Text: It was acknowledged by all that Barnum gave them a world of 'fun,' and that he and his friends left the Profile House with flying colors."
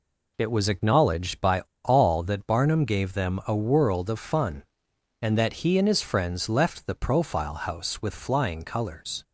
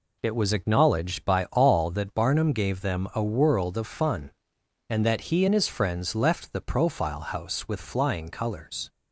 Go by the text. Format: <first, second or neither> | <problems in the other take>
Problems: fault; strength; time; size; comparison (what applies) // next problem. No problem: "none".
second | pauses between "by" and "all"; slight; at 1.6 s; 0.24 s long